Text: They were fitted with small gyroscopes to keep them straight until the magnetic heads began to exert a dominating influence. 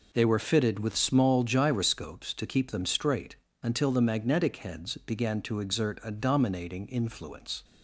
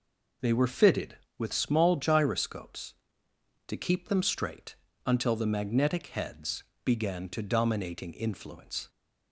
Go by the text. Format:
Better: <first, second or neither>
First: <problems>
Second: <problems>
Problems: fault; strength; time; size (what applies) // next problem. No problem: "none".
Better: first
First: pauses between "straight" and "until"; slight; at 3.3 s; 0.26 s long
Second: pauses between "straight" and "until"; slight; at 4.7 s; 0.30 s long // pauses between "heads" and "began"; slight; at 6.6 s; 0.20 s long // skips "exert a"; at 7.4 s